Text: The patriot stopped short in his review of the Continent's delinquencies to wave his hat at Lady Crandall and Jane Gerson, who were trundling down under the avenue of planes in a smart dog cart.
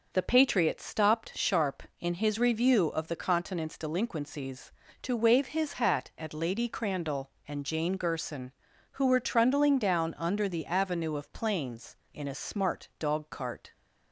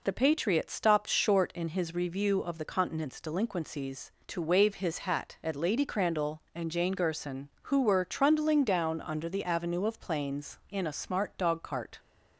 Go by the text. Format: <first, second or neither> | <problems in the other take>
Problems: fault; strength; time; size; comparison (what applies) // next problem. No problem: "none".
second | says "sharp" for "short"; at 1.3 s